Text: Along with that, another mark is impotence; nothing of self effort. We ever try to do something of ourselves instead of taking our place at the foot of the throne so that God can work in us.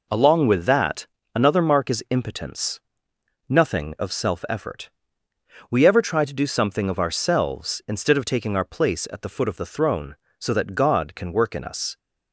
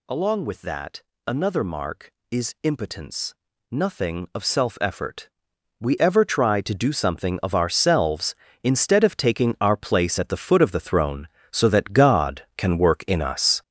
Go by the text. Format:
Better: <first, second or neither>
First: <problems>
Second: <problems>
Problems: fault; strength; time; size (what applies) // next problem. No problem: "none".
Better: first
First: none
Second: gets louder; strong; throughout; 8 dB